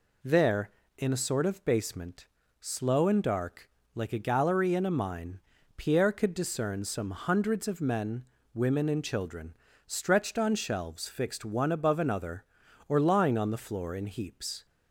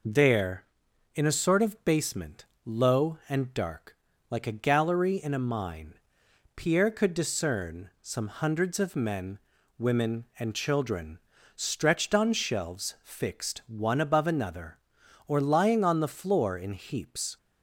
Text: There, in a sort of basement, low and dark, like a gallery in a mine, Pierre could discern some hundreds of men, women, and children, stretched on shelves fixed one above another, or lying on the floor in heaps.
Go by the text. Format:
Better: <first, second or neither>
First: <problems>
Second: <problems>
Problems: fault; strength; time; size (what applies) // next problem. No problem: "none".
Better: second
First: says "slow" for "low"; at 2.5 s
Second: none